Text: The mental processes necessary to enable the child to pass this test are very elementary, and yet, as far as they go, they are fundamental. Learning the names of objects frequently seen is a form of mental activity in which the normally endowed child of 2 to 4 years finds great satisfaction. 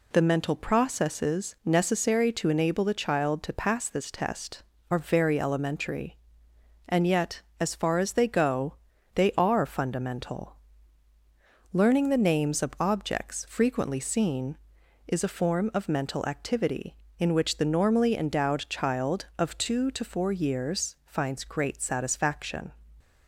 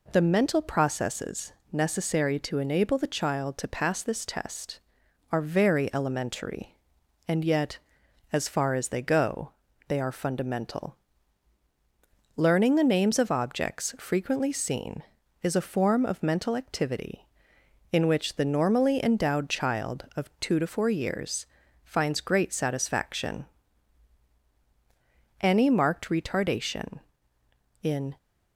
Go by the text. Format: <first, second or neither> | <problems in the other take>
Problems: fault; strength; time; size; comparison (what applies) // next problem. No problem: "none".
first | pauses between "processes" and "necessary"; slight; at 1.5 s; 0.20 s long // pauses between "years" and "finds"; slight; at 21.4 s; 0.36 s long // goes on to say "Any marked retardation in"; strong; from 25.4 s on; 2.7 s long